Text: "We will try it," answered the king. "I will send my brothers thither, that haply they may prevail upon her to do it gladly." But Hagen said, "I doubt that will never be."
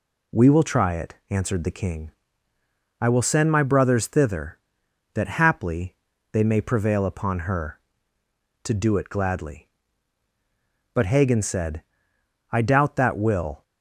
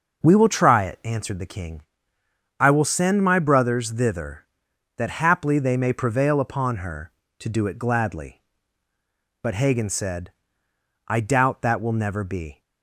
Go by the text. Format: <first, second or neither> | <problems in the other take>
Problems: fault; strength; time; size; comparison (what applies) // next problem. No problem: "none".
second | pauses between "haply" and "they"; at 5.9 s; 0.38 s long // stops before "never be"; at 13.6 s